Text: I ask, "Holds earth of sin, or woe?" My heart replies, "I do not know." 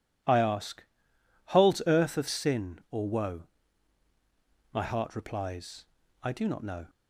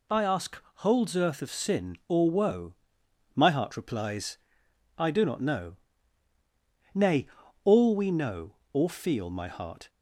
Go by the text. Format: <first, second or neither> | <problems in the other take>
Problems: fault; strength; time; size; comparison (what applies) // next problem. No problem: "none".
first | goes on to say "Nay all we know or feel my heart"; strong; from 6.9 s on; 2.9 s long